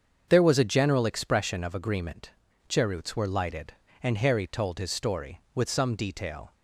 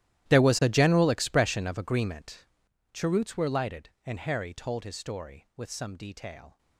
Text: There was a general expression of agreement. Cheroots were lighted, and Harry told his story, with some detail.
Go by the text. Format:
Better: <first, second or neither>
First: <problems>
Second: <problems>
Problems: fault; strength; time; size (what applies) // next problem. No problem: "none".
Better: first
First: starts louder than the rest; until 1.2 s; 7 dB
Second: gets quieter; strong; throughout; 19 dB // starts louder than the rest; strong; until 1.3 s; 13.5 dB